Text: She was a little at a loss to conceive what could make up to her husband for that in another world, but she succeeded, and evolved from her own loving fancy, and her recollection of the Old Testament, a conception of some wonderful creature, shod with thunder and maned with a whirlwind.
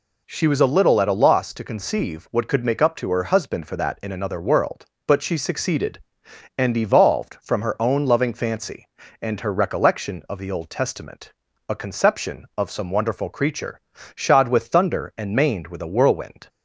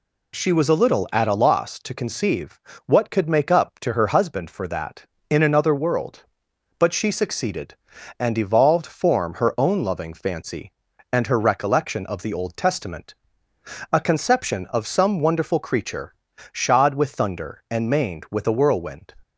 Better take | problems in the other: first | pauses between "conceive" and "what"; slight; at 2.5 s; 0.28 s long // says "form" for "from"; at 8.8 s

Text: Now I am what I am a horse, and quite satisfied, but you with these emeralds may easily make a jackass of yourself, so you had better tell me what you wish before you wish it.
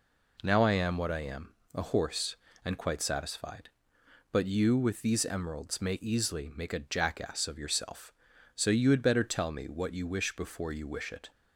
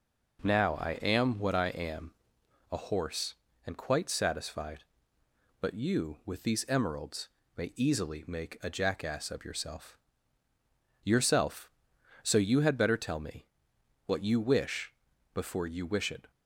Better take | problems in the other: first | pauses between "am" and "a"; noticeable; at 2.1 s; 0.60 s long; slight in the first // pauses between "emeralds" and "may"; slight; at 7.2 s; 0.30 s long // says "yourself" twice; at 11.0 s // pauses between "me" and "what"; noticeable; at 13.4 s; 0.62 s long // pauses between "wish" and "before"; at 14.9 s; 0.40 s long

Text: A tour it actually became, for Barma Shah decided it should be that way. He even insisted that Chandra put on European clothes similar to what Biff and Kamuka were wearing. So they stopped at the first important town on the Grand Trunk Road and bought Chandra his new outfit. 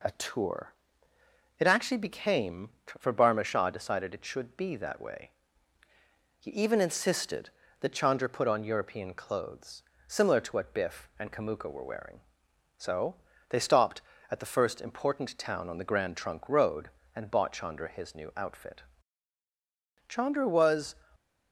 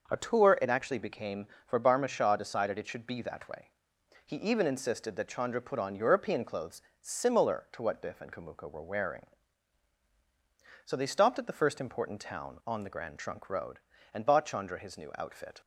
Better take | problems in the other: second | pauses between "tour" and "it"; noticeable; at 0.7 s; 0.84 s long // pauses between "clothes" and "similar"; slight; at 9.8 s; 0.26 s long; slight in the second // pauses between "So" and "they"; slight; at 13.1 s; 0.36 s long // goes on to say "Chandra was"; noticeable; from 20.0 s on; 0.88 s long // stays silent after the last word; slight; from 20.9 s on; 0.6 s long

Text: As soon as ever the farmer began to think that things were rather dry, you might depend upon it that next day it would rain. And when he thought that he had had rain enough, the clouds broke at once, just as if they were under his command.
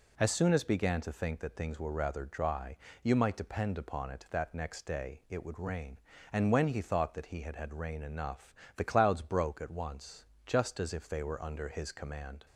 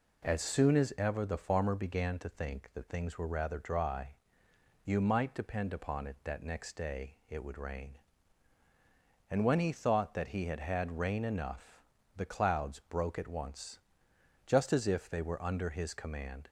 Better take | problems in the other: second | skips "ever the farmer"; at 0.6 s

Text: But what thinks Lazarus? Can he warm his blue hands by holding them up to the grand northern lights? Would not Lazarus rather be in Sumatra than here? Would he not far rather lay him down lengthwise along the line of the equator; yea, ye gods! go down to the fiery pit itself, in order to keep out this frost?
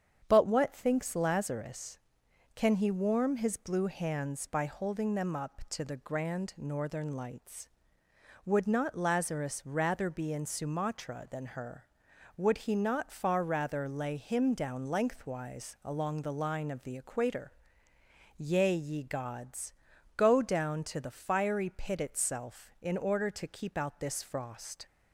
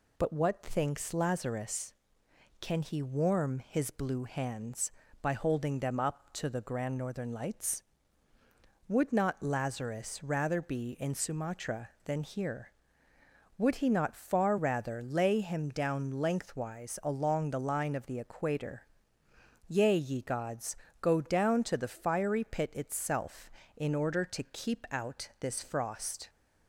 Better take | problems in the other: second | starts louder than the rest; strong; until 1.2 s; 8 dB // says "her" for "here"; at 11.4 s

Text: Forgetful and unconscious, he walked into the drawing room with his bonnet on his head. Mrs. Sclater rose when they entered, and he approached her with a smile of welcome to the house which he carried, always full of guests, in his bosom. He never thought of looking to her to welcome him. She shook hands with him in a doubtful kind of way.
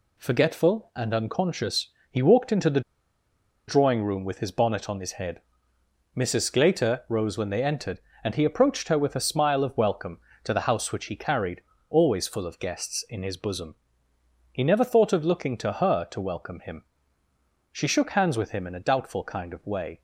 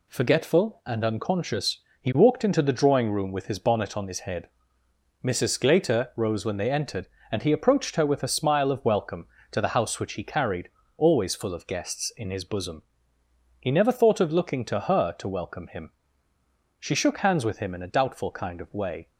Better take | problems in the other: second | pauses between "the" and "drawing"; noticeable; at 2.8 s; 0.87 s long

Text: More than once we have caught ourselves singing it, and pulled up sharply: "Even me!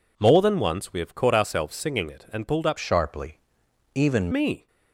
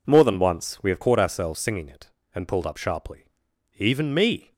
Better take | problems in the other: second | changes voice from "sharply" to "Even"; from 2.7 to 4.2 s; 1.5 s long

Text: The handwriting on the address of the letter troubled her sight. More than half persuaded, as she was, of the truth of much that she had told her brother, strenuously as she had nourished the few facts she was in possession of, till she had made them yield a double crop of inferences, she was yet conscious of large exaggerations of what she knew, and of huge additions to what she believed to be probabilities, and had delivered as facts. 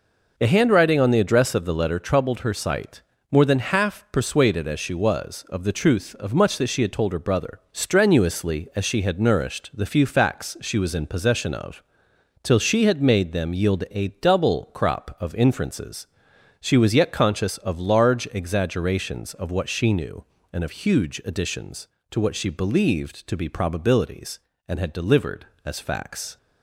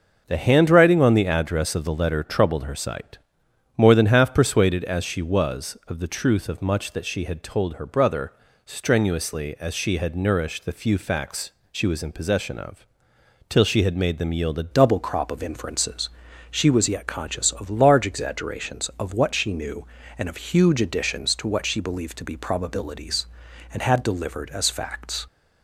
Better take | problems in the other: first | starts louder than the rest; noticeable; until 1.2 s; 6 dB // pauses between "facts" and "she"; slight; at 11.5 s; 0.20 s long // changes voice at "double"; from 14.7 s on; 10.5 s long

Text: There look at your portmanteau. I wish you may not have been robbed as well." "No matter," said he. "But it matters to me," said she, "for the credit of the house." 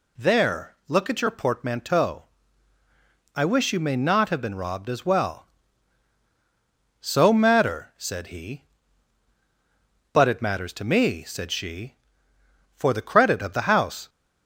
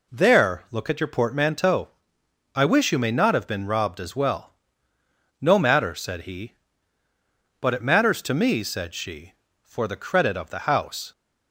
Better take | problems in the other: second | says "So" for "No"; at 7.0 s

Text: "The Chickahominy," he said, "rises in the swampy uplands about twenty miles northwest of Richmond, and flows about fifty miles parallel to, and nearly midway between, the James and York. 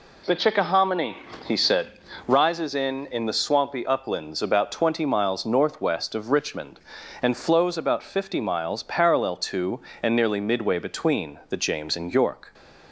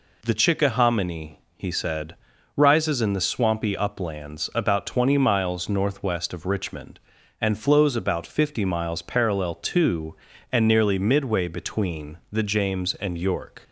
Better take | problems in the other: second | says "in" twice; at 3.0 s

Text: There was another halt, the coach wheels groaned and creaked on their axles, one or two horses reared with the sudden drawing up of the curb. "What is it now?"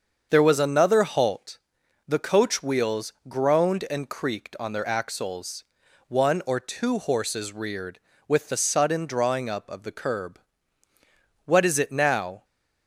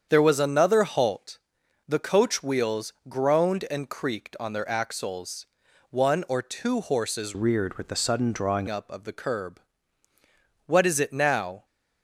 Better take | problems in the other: first | starts louder than the rest; strong; until 1.1 s; 7.5 dB; also in the first // pauses between "wheels" and "groaned"; slight; at 2.9 s; 0.16 s long; slight in the first // changes voice from "reared" to "drawing"; from 7.3 to 8.6 s; 1.3 s long

